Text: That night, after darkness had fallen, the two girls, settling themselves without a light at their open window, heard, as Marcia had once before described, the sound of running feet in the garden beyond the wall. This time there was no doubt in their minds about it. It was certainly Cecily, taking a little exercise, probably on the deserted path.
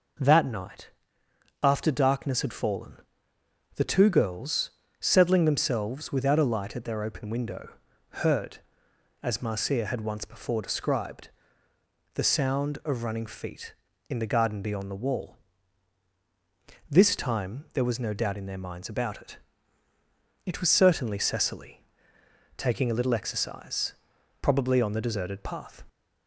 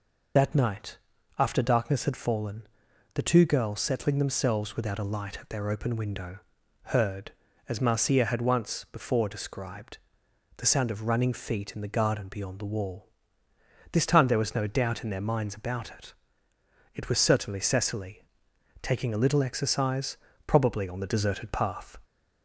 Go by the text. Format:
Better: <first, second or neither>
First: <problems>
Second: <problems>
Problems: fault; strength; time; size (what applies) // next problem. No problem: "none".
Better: first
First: none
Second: loses the start of "That"; at 0.3 s; 65 ms